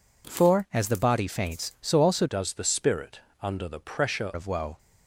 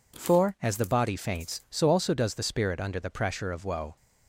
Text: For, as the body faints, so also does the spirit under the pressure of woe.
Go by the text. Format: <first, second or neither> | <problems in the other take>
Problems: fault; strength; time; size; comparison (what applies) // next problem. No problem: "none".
second | changes voice from "does" to "pressure"; from 2.2 to 4.3 s; 2.1 s long // pauses between "spirit" and "under"; slight; at 3.2 s; 0.22 s long